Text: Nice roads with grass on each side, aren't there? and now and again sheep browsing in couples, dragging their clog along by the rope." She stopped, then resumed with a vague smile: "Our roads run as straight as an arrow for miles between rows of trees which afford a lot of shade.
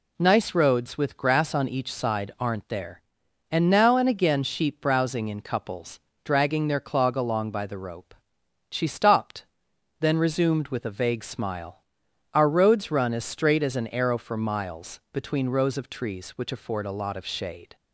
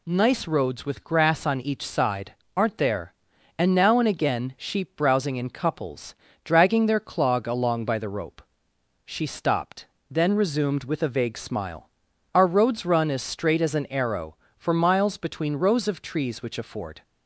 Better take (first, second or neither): first